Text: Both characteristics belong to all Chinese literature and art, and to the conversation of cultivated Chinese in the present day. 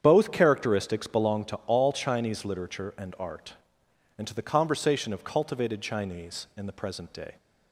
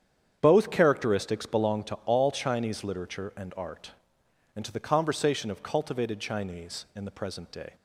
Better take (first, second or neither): neither